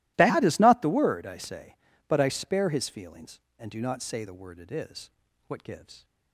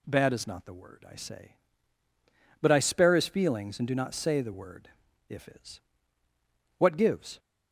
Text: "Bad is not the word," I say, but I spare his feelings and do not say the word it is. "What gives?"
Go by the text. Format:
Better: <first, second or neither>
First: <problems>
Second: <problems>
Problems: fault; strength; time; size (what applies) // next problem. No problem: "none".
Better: first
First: none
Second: says "if" for "it"; at 5.2 s